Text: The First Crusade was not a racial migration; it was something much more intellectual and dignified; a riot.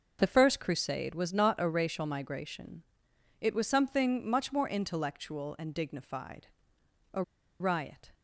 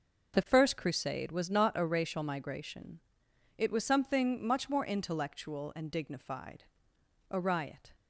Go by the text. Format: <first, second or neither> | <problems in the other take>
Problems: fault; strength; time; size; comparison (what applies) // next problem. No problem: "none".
second | starts louder than the rest; until 1.2 s; 6 dB; also in the second // pauses between "a" and "riot"; at 7.2 s; 0.38 s long